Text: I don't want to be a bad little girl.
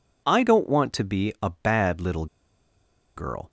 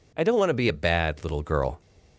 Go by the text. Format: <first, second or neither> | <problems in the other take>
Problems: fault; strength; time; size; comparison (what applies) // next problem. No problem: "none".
second | pauses between "little" and "girl"; noticeable; at 2.2 s; 0.91 s long